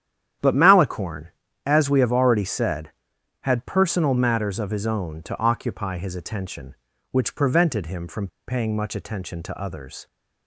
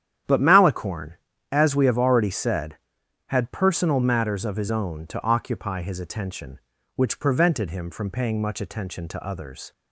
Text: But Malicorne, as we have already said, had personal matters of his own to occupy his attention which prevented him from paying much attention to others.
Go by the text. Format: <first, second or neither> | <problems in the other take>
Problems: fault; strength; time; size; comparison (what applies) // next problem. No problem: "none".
second | starts louder than the rest; strong; until 1.7 s; 10 dB; strong in the second // pauses between "from" and "paying"; slight; at 8.2 s; 0.20 s long